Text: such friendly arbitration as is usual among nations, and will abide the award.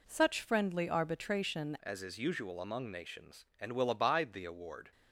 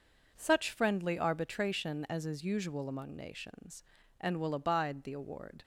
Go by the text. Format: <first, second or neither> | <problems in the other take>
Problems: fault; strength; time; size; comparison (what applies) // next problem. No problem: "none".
second | changes voice at "as"; from 1.8 s on; 3.1 s long